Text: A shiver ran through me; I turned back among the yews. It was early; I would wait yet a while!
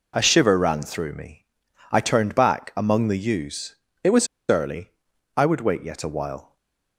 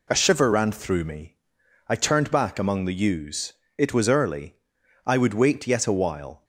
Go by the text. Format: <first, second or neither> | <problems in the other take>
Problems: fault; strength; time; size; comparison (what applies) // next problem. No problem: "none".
second | pauses between "was" and "early"; slight; at 4.2 s; 0.23 s long // stays silent after the last word; slight; from 6.4 s on; 0.5 s long